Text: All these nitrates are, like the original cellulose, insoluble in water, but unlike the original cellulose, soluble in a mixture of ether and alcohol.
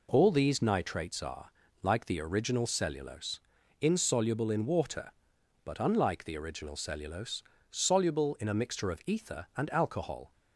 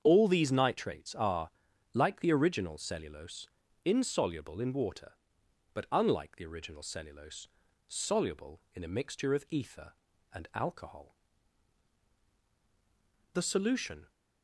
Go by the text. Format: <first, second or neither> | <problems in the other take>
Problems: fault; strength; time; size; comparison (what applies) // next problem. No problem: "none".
first | starts louder than the rest; strong; until 1.0 s; 7.5 dB // goes on to say "The solution"; noticeable; from 13.3 s on; 0.76 s long